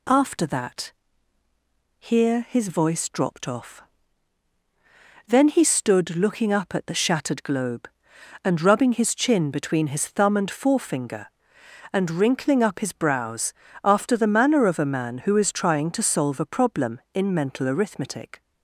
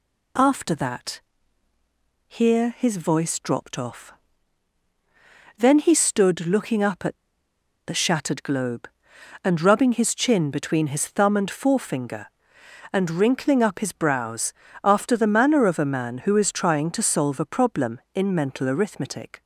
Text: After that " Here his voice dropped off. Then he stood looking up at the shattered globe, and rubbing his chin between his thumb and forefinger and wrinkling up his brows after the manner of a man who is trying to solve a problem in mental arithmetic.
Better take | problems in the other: first | pauses between "at" and "the"; noticeable; at 7.1 s; 0.69 s long // pauses between "brows" and "after"; slight; at 14.5 s; 0.30 s long; slight in the first

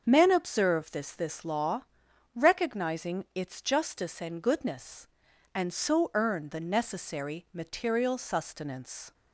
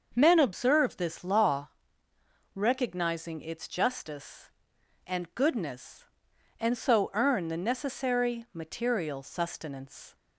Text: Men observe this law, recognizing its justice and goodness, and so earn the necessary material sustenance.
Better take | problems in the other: second | starts louder than the rest; until 1.0 s; 6.5 dB; also in the second // says "this" twice; at 1.1 s

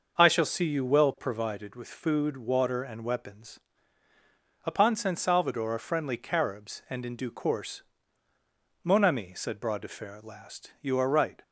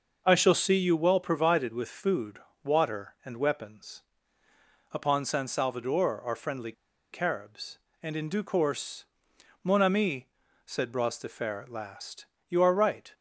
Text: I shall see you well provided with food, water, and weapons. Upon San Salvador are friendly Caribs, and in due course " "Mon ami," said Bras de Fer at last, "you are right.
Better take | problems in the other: first | starts louder than the rest; noticeable; until 1.2 s; 6 dB; noticeable in the first // pauses between "friendly" and "Caribs"; at 6.7 s; 0.40 s long

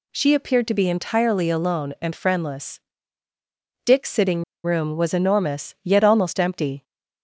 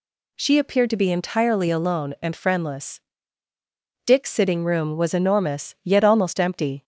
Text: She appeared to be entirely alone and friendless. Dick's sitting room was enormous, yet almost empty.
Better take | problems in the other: second | pauses between "sitting" and "room"; slight; at 4.4 s; 0.20 s long

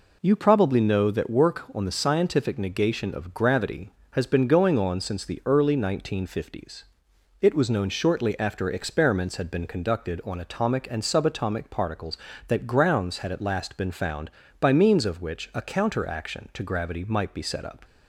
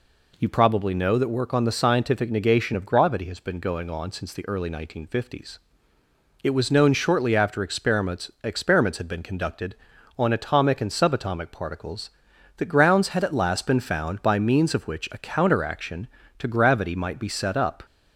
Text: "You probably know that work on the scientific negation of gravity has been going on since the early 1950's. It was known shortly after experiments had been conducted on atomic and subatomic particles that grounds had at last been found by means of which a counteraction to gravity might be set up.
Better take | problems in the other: first | says "experiments" twice; at 8.4 s

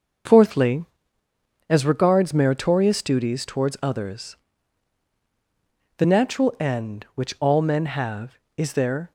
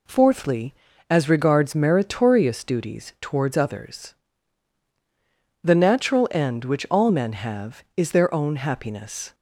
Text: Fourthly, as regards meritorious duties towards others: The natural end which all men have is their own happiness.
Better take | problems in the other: second | starts louder than the rest; noticeable; until 2.1 s; 6 dB // stops before "own happiness"; at 9.0 s

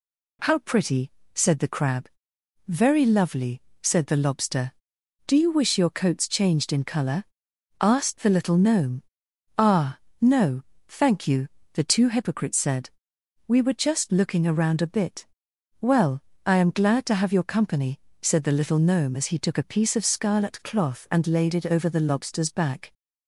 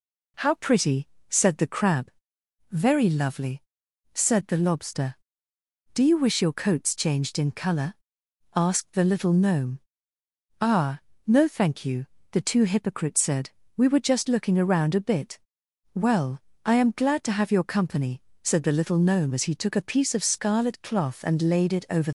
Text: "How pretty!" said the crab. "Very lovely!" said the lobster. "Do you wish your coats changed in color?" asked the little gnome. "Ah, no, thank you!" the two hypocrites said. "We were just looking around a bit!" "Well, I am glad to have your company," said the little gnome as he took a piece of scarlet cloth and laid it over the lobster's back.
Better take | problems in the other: first | stops before "the lobster's back"; at 22.0 s

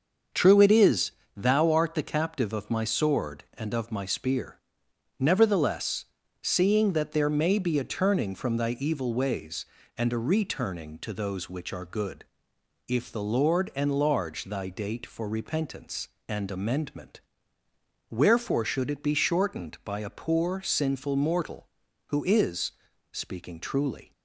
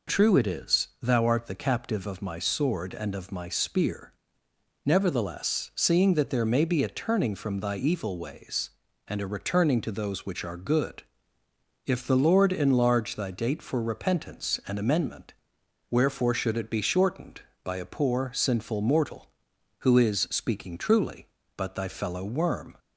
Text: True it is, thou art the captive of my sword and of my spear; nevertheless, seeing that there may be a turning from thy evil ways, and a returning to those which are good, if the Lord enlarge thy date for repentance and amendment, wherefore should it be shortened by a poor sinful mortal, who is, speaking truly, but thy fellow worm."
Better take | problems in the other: second | starts louder than the rest; until 1.5 s; 6.5 dB // stops before "but thy fellow worm"; at 24.1 s

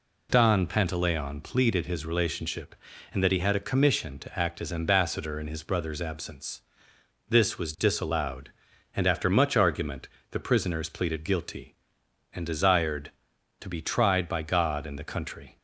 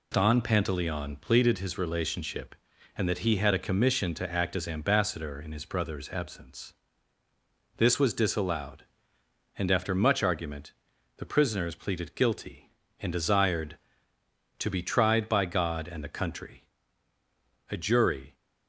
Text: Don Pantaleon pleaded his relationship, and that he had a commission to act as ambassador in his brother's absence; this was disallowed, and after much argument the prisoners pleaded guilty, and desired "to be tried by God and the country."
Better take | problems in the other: first | pauses between "argument" and "the"; at 10.7 s; 0.42 s long; slight in the first // goes on to say "A jury"; noticeable; from 17.6 s on; 0.66 s long

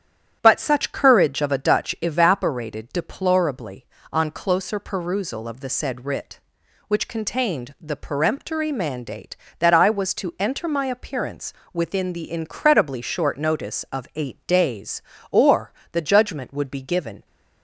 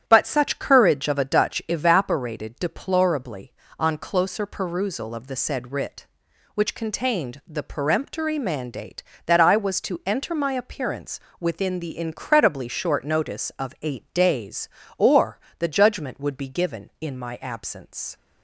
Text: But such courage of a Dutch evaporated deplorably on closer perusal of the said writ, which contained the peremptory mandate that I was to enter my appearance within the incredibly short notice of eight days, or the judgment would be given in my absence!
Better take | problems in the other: second | starts louder than the rest; strong; until 1.4 s; 10 dB; strong in the second // pauses between "appearance" and "within"; slight; at 11.5 s; 0.22 s long; slight in the second // pauses between "or" and "the"; slight; at 15.7 s; 0.18 s long; slight in the second // stops before "in my absence"; at 17.2 s

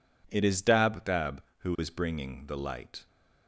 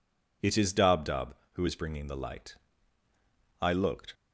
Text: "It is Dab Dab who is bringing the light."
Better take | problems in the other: first | goes on to say "I looked"; from 3.5 s on; 0.54 s long

